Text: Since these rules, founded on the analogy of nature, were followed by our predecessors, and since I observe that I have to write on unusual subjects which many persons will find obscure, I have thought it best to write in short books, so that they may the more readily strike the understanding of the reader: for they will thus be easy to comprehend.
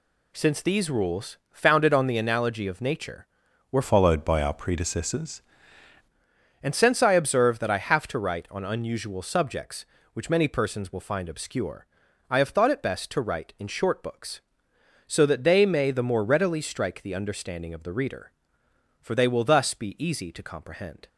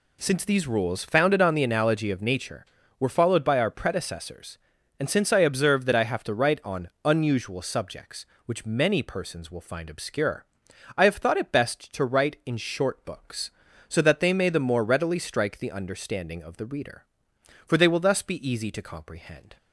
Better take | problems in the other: second | changes voice from "followed" to "predecessors"; from 3.8 to 5.4 s; 1.6 s long

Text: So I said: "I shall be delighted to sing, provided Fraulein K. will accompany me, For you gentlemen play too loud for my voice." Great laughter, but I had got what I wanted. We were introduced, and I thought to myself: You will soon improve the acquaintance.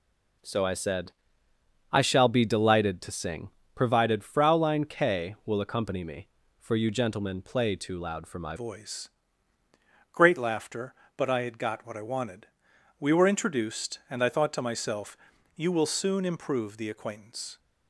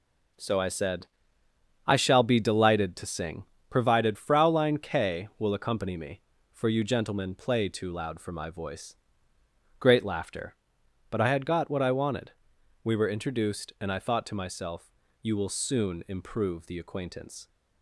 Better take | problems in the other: second | changes voice at "voice"; from 8.5 s on; 9.0 s long

